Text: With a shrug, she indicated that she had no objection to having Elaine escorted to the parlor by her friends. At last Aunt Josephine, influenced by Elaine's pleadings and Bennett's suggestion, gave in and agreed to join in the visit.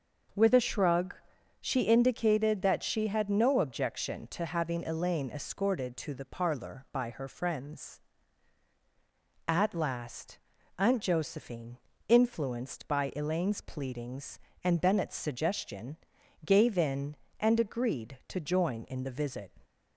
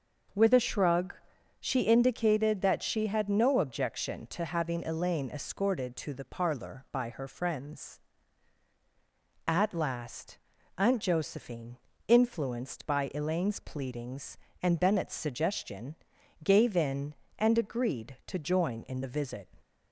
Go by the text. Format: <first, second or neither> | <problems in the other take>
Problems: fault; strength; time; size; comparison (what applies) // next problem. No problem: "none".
neither | starts louder than the rest; the same in both // pauses between "last" and "Aunt"; the same in both